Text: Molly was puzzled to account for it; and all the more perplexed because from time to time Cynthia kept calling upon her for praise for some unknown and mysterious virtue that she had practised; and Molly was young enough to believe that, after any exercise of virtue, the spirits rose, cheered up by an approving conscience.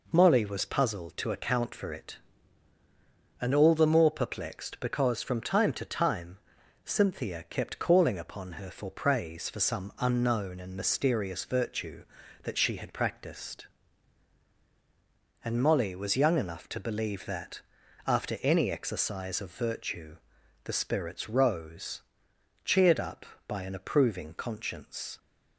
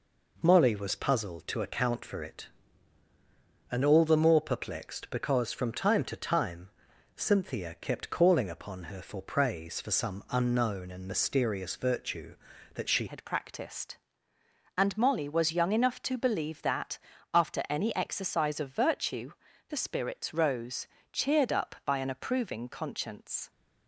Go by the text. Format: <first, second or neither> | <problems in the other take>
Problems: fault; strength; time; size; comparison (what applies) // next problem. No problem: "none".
first | pauses between "time" and "Cynthia"; noticeable; at 6.6 s; 0.46 s long; noticeable in the first // changes voice at "had"; from 13.0 s on; 10.4 s long